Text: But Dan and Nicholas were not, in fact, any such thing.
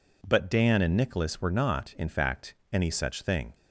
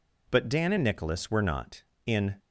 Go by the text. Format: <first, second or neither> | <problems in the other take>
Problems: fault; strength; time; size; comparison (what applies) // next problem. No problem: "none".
first | stops before "fact any such thing"; at 2.3 s